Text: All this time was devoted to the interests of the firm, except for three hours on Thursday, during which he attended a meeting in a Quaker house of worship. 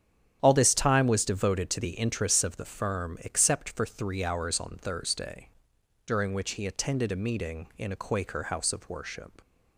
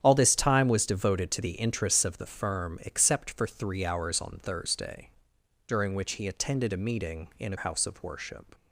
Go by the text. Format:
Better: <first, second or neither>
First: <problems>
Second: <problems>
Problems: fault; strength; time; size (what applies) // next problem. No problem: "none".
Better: first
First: starts louder than the rest; strong; until 1.4 s; 9.5 dB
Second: starts louder than the rest; strong; until 1.0 s; 9.5 dB // skips "Quaker"; at 7.5 s